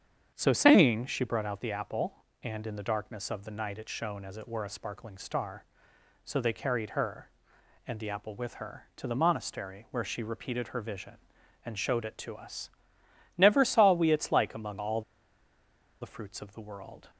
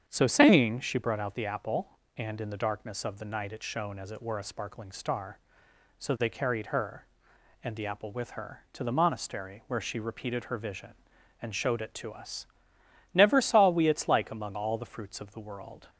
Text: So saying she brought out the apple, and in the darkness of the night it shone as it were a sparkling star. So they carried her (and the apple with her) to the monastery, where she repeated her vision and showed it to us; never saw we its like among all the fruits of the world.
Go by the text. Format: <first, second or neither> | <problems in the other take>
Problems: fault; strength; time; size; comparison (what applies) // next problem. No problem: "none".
second | starts louder than the rest; strong; until 1.3 s; 8.5 dB; strong in the second // pauses between "all" and "the"; at 15.0 s; 1.0 s long